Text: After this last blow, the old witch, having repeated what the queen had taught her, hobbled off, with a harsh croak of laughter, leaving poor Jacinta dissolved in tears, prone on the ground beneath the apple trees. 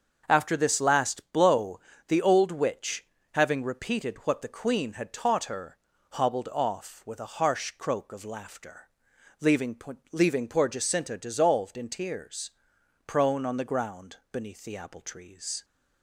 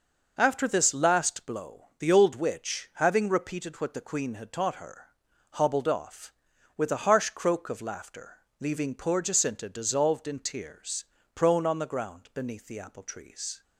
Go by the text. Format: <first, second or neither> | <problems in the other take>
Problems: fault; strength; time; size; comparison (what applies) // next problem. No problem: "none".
second | starts louder than the rest; until 1.2 s; 6.5 dB // says "leaving" twice; at 10.1 s // pauses between "ground" and "beneath"; slight; at 14.1 s; 0.16 s long